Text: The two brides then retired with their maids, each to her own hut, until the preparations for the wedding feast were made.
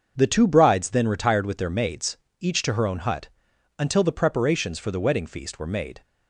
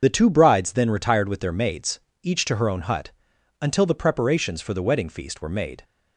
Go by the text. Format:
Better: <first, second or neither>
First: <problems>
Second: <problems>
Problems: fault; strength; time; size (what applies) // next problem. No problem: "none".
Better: first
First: starts louder than the rest; until 1.1 s; 6.5 dB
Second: loses the start of "The"; at 0.0 s; 50 ms // starts louder than the rest; until 1.0 s; 6.5 dB